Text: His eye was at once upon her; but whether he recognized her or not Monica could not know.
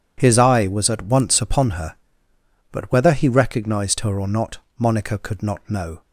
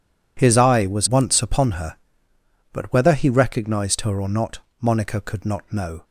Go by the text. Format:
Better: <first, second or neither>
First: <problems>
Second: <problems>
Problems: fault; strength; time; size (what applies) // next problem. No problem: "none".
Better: first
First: pauses between "not" and "Monica"; slight; at 4.5 s; 0.22 s long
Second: skips "at"; at 1.0 s // pauses between "not" and "Monica"; slight; at 4.5 s; 0.24 s long